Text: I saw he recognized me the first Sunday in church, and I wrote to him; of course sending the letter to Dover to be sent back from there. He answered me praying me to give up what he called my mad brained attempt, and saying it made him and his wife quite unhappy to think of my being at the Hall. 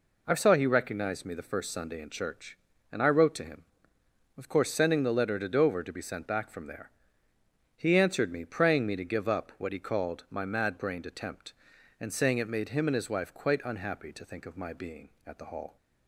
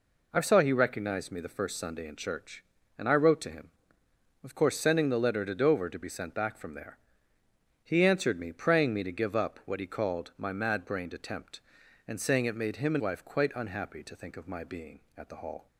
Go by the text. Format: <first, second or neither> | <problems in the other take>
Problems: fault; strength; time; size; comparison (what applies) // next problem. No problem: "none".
first | skips "his"; at 13.0 s